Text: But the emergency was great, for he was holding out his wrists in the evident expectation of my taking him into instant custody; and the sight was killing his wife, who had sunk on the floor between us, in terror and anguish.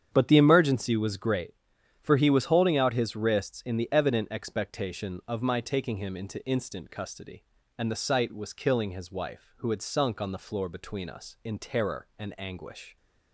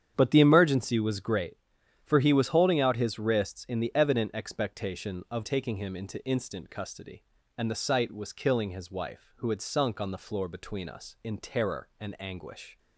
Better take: first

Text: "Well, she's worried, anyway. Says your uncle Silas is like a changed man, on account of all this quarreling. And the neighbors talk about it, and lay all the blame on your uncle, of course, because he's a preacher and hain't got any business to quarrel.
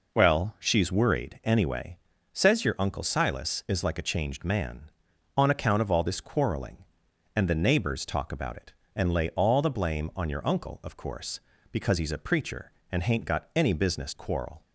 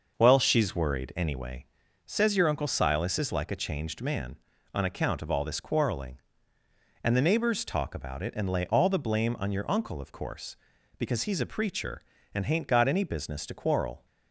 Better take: second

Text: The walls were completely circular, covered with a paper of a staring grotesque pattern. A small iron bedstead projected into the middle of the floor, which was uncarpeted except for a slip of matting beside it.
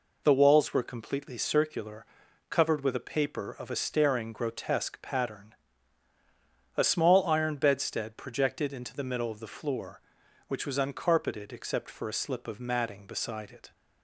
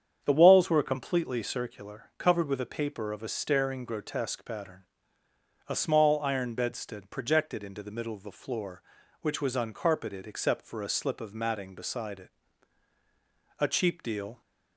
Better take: first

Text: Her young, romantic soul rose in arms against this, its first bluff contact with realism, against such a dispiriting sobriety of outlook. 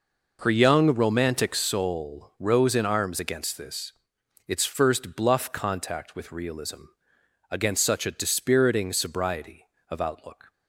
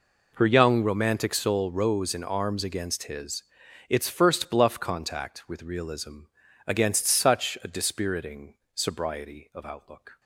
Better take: first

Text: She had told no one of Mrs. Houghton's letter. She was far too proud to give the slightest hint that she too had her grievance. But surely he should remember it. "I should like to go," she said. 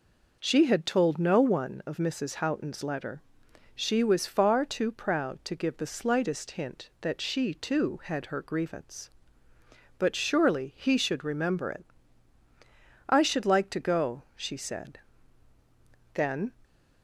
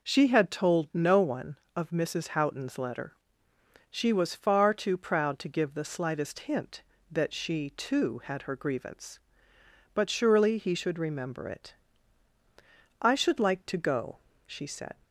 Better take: second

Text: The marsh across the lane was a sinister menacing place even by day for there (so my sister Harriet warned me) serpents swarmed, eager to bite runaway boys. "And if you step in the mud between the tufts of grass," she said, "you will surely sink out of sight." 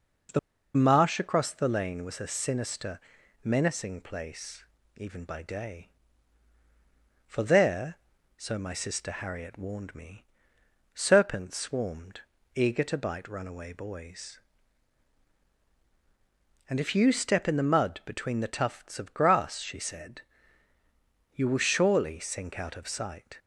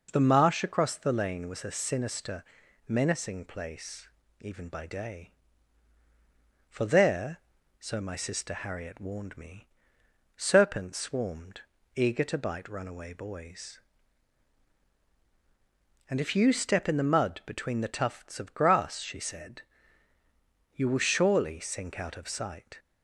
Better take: second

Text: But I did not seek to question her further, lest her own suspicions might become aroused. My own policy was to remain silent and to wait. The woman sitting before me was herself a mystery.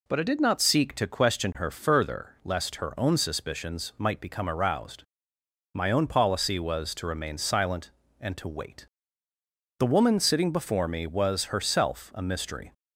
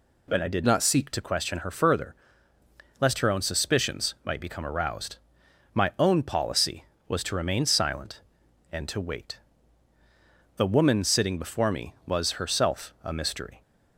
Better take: first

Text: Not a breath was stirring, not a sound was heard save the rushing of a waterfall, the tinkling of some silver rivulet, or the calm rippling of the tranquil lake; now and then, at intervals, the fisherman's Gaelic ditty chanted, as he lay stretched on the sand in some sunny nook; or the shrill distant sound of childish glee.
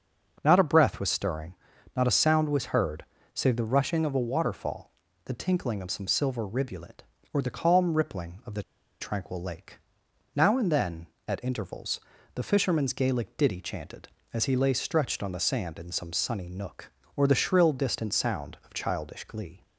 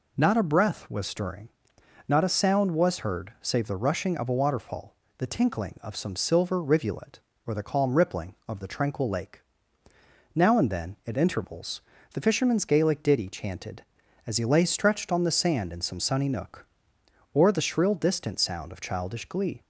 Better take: second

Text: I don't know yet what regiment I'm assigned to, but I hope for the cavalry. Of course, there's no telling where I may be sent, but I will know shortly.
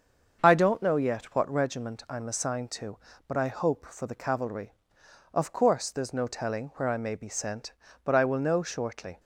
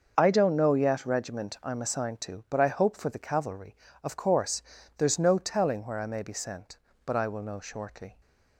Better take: first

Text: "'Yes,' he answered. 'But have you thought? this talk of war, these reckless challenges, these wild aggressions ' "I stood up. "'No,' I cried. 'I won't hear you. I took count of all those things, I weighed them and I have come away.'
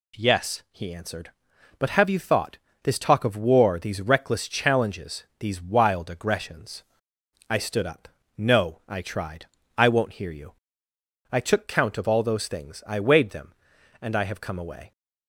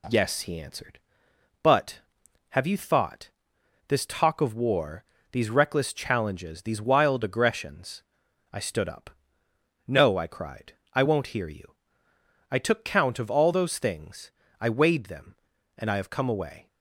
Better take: second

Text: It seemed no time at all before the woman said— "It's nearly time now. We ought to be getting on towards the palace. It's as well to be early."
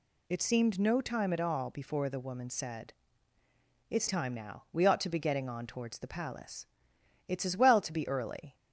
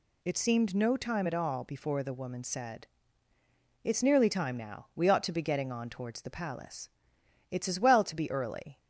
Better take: second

